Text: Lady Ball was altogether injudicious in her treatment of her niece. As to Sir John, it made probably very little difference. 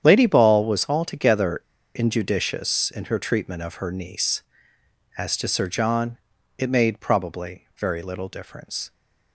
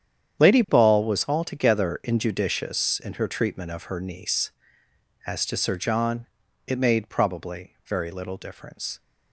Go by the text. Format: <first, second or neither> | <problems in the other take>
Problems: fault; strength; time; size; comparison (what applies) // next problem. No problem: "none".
second | starts louder than the rest; strong; until 1.0 s; 9 dB; strong in the second // pauses between "altogether" and "injudicious"; slight; at 1.5 s; 0.35 s long